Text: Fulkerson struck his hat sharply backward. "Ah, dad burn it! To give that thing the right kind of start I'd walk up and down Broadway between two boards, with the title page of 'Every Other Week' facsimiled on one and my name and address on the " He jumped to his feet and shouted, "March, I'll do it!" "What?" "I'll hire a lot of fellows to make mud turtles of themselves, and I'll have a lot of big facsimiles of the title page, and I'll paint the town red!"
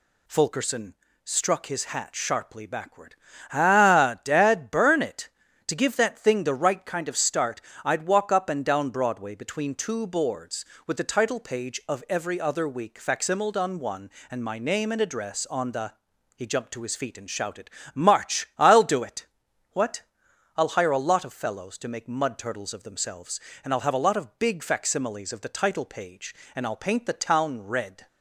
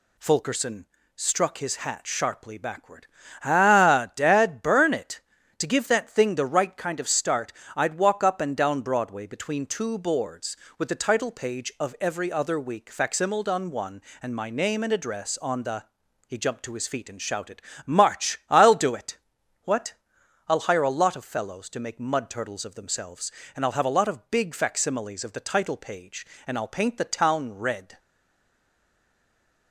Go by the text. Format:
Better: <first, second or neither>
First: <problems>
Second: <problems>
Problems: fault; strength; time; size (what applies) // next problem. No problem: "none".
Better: first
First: pauses between "Fulkerson" and "struck"; slight; at 0.9 s; 0.30 s long // pauses between "start" and "I'd"; slight; at 7.6 s; 0.22 s long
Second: pauses between "Fulkerson" and "struck"; slight; at 0.8 s; 0.30 s long // pauses between "start" and "I'd"; slight; at 7.5 s; 0.22 s long // stays silent after the last word; noticeable; from 27.9 s on; 1.8 s long